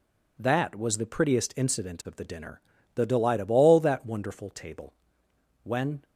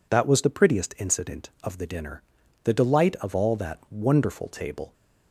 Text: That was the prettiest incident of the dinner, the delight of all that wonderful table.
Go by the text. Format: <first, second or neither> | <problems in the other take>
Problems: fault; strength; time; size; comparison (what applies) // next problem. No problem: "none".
second | goes on to say "When"; slight; from 5.6 s on; 0.40 s long